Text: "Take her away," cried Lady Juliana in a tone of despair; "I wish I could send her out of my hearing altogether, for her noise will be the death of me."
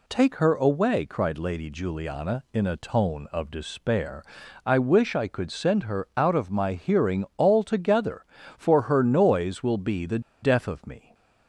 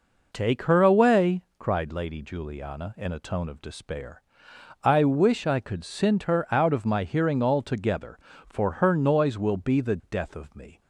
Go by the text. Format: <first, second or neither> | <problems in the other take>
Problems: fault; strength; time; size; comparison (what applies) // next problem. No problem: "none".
second | pauses between "the" and "death"; slight; at 10.1 s; 0.22 s long